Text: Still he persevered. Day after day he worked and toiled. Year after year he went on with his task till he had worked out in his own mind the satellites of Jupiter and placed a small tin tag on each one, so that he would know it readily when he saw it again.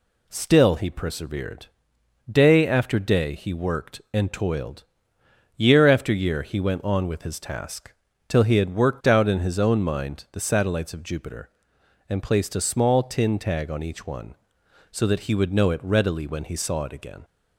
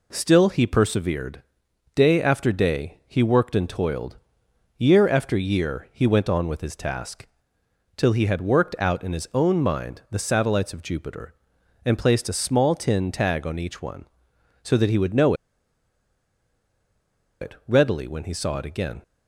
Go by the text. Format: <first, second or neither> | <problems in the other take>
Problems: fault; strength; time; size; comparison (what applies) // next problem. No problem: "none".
first | pauses between "task" and "till"; noticeable; at 7.2 s; 0.68 s long; slight in the first // pauses between "know" and "it"; strong; at 15.3 s; 2.0 s long